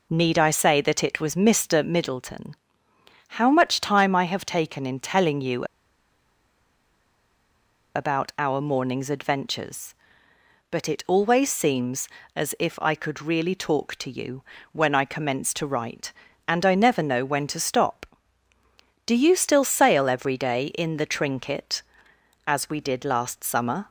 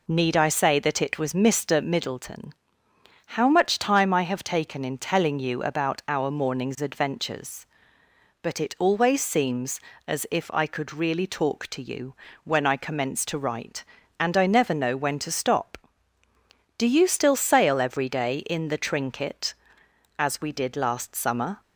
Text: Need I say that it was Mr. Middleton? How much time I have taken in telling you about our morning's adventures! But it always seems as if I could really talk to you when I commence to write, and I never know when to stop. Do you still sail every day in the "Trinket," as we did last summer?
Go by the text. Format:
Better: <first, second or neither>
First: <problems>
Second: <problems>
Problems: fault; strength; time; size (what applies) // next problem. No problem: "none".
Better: second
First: pauses between "you" and "about"; strong; at 5.6 s; 2.2 s long // pauses between "you" and "when"; slight; at 14.4 s; 0.30 s long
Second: pauses between "you" and "when"; slight; at 12.1 s; 0.30 s long